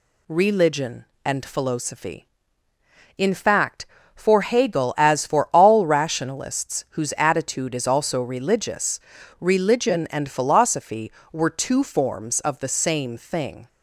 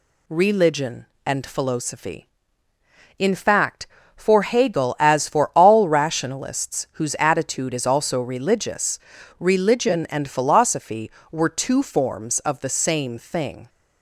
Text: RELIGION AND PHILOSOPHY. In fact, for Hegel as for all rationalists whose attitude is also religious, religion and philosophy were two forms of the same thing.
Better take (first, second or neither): neither